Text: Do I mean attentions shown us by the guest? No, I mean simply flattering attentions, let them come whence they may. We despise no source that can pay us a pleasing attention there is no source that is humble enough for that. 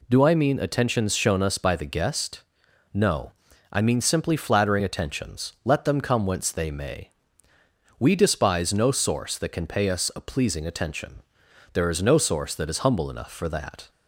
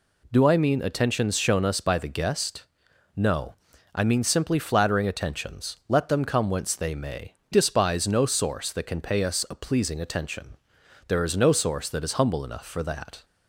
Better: first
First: pauses between "attention" and "there"; noticeable; at 11.2 s; 0.50 s long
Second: skips "We"; at 7.4 s // pauses between "attention" and "there"; noticeable; at 10.5 s; 0.50 s long

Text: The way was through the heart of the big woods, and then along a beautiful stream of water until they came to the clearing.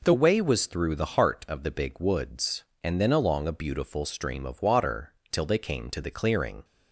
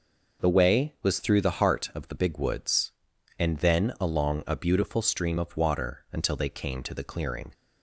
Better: second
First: says "till" for "until"; at 5.3 s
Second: none

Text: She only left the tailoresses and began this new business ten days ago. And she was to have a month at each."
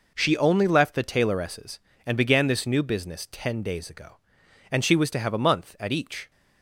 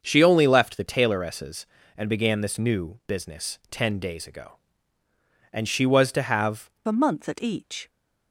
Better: first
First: none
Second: starts louder than the rest; until 1.0 s; 7 dB // changes voice at "a"; from 6.8 s on; 1.0 s long

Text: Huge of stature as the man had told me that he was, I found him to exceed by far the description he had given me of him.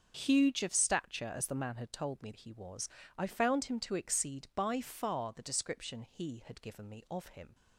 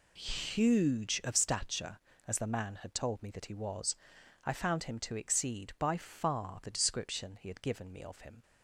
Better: second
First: starts louder than the rest; until 1.1 s; 6.5 dB // skips "that"; at 2.3 s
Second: none

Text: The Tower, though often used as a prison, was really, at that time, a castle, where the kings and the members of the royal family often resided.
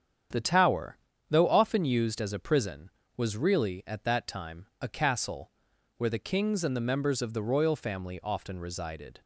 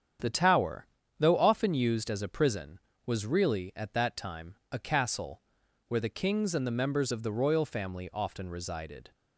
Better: neither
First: starts louder than the rest; strong; until 1.6 s; 8.5 dB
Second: starts louder than the rest; strong; until 1.5 s; 8.5 dB

